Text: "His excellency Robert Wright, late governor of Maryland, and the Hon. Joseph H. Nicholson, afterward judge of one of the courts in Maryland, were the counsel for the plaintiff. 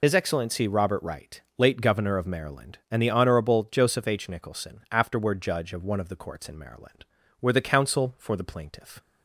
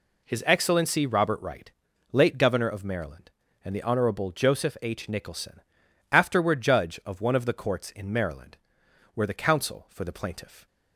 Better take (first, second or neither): second